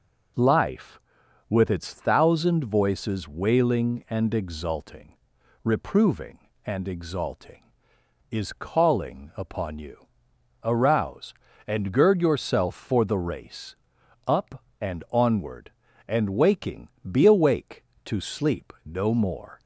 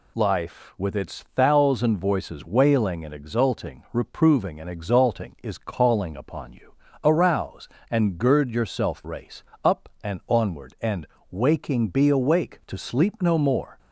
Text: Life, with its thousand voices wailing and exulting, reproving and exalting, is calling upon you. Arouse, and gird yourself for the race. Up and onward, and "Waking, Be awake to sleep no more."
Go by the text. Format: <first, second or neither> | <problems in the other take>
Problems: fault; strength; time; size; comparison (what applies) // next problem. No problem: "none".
first | skips "for the"; at 9.0 s // pauses between "and" and "Waking"; slight; at 11.0 s; 0.24 s long